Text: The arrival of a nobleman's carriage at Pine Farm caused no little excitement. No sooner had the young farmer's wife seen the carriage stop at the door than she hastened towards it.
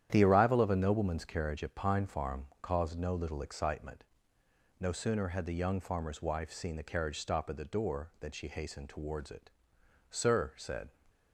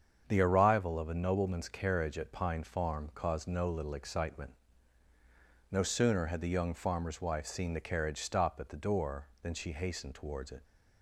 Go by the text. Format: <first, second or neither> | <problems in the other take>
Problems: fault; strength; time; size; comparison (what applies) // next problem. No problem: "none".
second | starts louder than the rest; strong; until 1.1 s; 10.5 dB; strong in the second // pauses between "Farm" and "caused"; slight; at 2.4 s; 0.16 s long // goes on to say "Sir said"; noticeable; from 10.0 s on; 0.80 s long